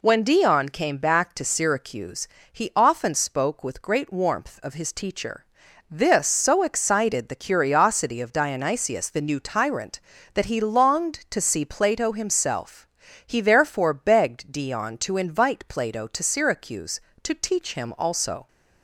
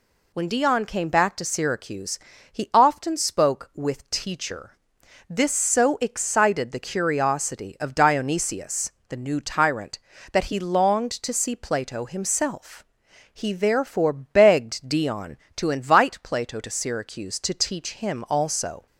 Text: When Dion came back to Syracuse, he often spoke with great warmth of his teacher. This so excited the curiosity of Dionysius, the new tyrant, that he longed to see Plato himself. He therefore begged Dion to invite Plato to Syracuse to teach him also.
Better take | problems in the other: first | skips "great warmth of his"; at 4.0 s

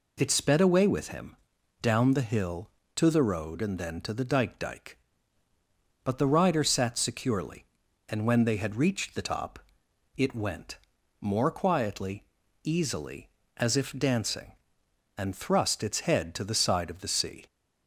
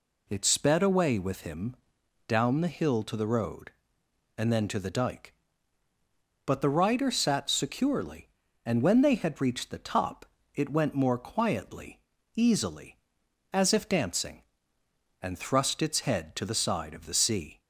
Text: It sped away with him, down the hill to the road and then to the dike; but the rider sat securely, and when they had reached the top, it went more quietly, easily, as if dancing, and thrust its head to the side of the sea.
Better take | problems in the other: second | says "dike" twice; at 4.5 s // pauses between "went" and "more"; at 10.7 s; 0.42 s long

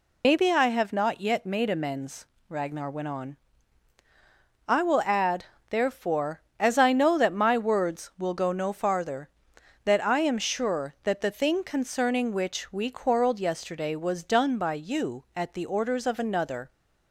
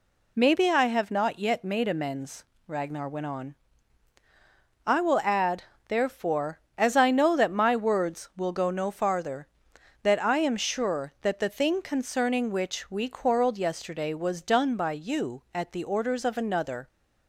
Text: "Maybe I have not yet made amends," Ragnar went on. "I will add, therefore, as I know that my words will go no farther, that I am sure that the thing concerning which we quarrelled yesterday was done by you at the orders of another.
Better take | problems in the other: second | loses the start of "Maybe"; at 0.2 s; 70 ms

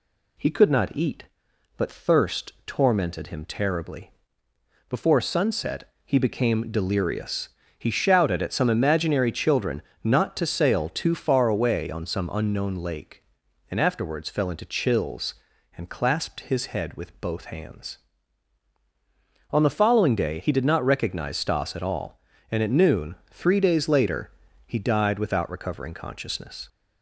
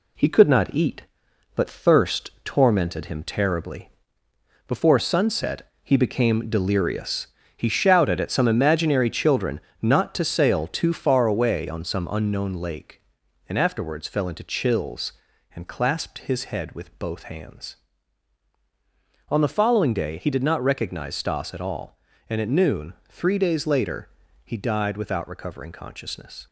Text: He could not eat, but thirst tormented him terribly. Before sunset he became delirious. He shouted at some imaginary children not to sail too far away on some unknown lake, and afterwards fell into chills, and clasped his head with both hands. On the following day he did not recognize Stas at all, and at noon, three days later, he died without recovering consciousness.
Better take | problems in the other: first | gets quieter; noticeable; throughout; 5.5 dB // pauses between "children" and "not"; slight; at 9.6 s; 0.20 s long; slight in the first

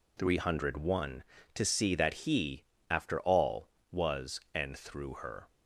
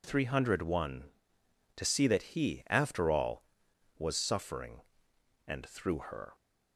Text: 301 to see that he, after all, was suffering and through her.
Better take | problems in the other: second | skips "suffering"; at 4.4 s

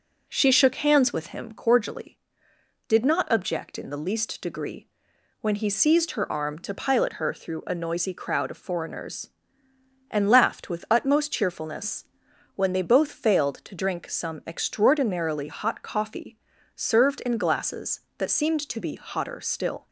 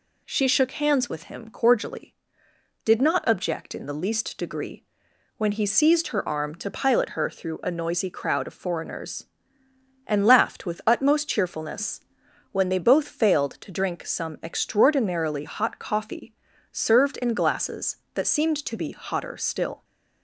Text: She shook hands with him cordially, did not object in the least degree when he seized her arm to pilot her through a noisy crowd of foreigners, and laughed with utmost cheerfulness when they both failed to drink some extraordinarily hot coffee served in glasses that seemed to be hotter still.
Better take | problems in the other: second | starts louder than the rest; noticeable; until 1.6 s; 4.5 dB // pauses between "degree" and "when"; noticeable; at 4.8 s; 0.52 s long; noticeable in the second // pauses between "cheerfulness" and "when"; noticeable; at 12.0 s; 0.52 s long; noticeable in the second // pauses between "coffee" and "served"; at 16.3 s; 0.40 s long; also in the second

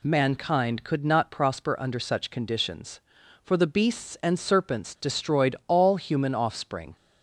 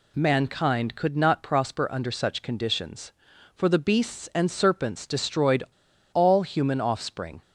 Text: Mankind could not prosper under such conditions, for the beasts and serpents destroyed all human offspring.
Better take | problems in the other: first | pauses between "destroyed" and "all"; noticeable; at 5.6 s; 0.48 s long

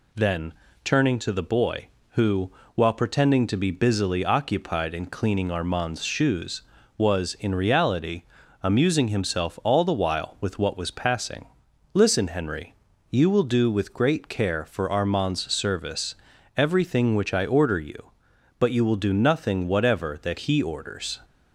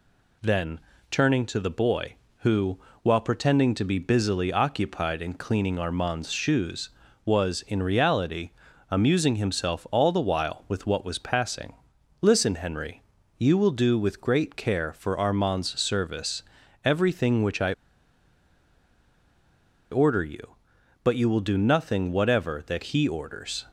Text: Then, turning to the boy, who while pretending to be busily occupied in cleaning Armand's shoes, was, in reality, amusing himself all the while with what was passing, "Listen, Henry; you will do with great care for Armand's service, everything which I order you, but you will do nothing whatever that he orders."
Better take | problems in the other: first | pauses between "who" and "while"; slight; at 2.7 s; 0.24 s long; slight in the first // pauses between "I" and "order"; strong; at 17.7 s; 2.1 s long

